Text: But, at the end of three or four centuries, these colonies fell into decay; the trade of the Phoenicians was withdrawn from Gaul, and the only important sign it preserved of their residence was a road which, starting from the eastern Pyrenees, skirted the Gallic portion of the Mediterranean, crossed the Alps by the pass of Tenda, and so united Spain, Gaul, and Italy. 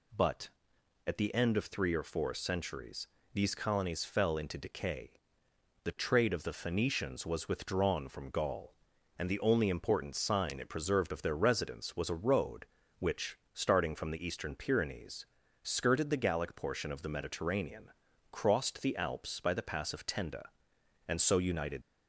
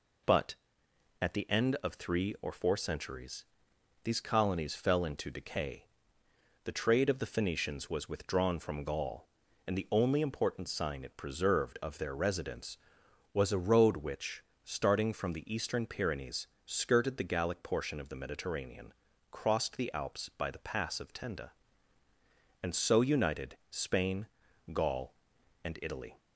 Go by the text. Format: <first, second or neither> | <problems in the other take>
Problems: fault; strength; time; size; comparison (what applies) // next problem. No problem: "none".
second | stops before "Spain Gaul and Italy"; at 21.8 s